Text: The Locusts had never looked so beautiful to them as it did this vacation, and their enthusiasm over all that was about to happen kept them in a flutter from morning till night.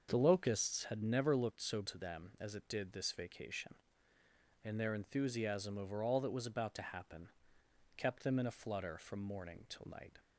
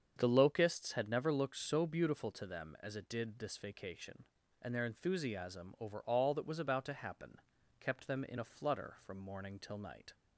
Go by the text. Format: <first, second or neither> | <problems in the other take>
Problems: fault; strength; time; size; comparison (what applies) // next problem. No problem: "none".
second | starts louder than the rest; until 1.1 s; 6.5 dB; strong in the second // skips "beautiful"; at 1.8 s // pauses between "happen" and "kept"; noticeable; at 7.3 s; 0.66 s long; also in the second